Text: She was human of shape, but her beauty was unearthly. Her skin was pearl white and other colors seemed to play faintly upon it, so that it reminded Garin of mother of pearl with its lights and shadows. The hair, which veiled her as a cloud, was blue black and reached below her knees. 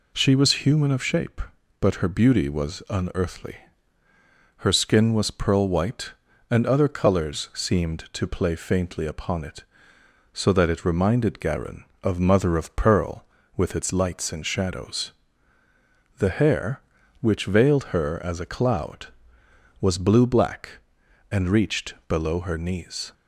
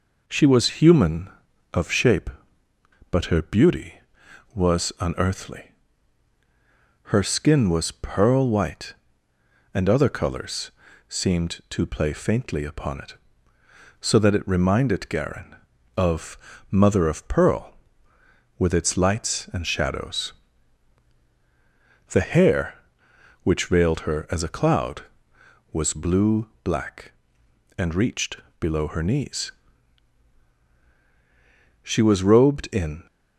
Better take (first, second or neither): first